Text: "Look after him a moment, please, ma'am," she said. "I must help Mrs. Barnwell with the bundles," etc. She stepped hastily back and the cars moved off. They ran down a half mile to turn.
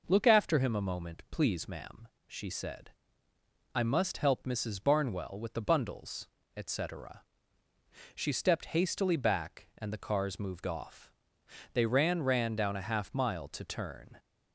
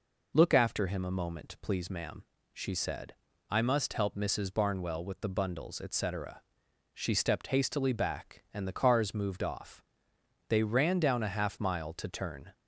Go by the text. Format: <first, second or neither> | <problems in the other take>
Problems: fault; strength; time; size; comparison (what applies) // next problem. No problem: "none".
second | says "ran" twice; at 12.2 s